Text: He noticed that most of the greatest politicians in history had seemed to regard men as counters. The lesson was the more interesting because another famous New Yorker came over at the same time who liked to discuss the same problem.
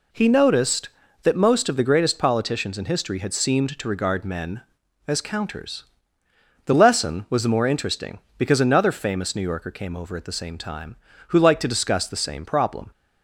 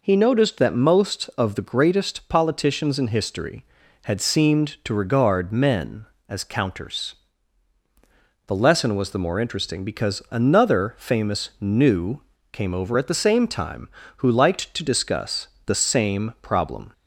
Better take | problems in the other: first | skips "Yorker"; at 12.3 s // pauses between "discuss" and "the"; slight; at 15.4 s; 0.18 s long

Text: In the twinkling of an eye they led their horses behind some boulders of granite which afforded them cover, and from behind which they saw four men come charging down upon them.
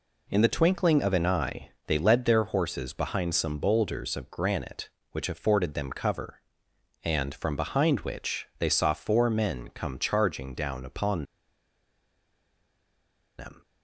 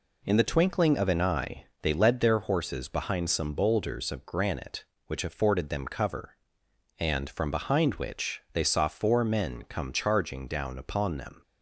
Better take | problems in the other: second | pauses between "eye" and "they"; slight; at 1.7 s; 0.16 s long; slight in the second // pauses between "upon" and "them"; strong; at 11.2 s; 2.1 s long

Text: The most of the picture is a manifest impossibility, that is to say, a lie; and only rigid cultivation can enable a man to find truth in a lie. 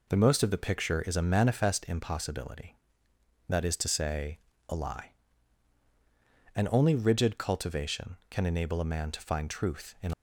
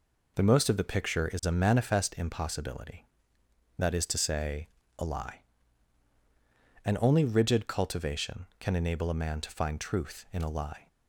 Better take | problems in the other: second | stops before "a lie"; at 10.1 s

